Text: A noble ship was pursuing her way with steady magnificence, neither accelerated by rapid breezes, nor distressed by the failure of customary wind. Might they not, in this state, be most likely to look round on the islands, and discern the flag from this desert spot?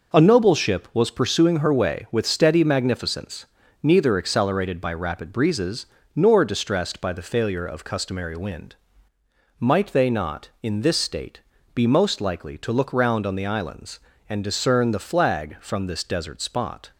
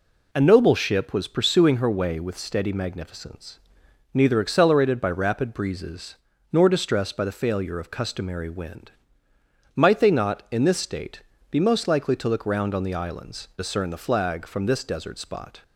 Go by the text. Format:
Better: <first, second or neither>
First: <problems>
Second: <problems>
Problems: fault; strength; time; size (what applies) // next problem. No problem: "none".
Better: first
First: none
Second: skips "and"; at 13.5 s